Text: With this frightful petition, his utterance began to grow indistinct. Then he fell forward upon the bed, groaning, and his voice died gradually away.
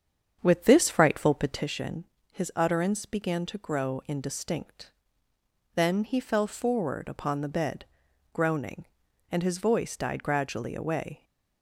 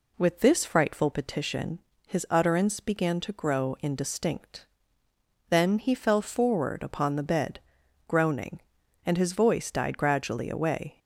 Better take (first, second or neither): second